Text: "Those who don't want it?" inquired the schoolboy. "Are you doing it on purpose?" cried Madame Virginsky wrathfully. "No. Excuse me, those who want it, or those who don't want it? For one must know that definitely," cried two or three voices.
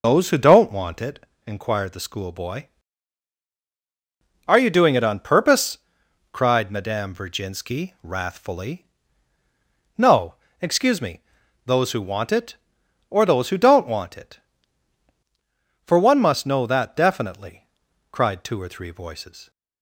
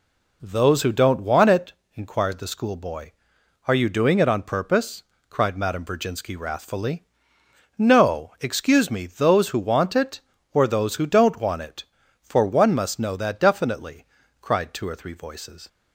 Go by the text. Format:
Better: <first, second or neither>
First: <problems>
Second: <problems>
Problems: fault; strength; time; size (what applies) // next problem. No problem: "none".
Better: second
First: loses the start of "Those"; at 0.0 s; 40 ms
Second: none